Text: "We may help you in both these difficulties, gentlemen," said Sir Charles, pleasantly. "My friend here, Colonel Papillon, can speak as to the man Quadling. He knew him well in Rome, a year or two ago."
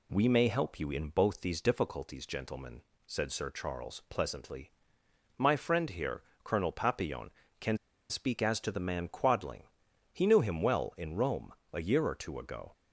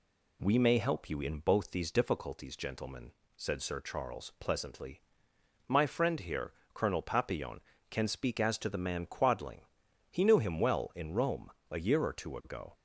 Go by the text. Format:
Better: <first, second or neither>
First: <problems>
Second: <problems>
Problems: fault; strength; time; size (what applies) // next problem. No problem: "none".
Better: second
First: pauses between "can" and "speak"; slight; at 7.7 s; 0.33 s long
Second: none